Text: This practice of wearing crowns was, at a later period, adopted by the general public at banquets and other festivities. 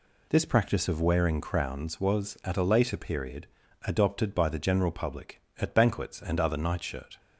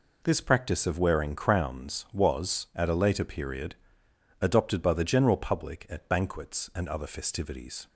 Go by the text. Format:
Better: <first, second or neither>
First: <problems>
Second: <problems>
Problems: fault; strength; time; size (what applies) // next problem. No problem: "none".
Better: second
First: says "nightshirt" for "festivities"; at 6.5 s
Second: none